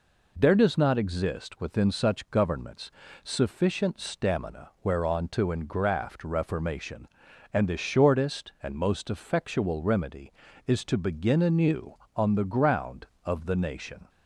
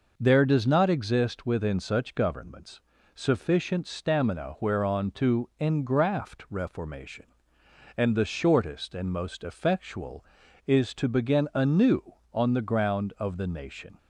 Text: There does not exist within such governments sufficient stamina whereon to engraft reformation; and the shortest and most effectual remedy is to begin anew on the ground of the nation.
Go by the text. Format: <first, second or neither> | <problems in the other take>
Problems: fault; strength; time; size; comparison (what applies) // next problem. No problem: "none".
first | pauses between "governments" and "sufficient"; slight; at 2.7 s; 0.36 s long; slight in the first // skips "remedy"; at 10.4 s